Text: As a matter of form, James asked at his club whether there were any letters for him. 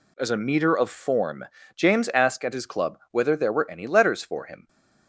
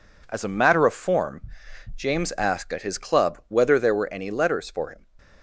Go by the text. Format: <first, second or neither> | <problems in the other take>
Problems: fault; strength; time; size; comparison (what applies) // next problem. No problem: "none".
second | says "meter" for "matter"; at 0.3 s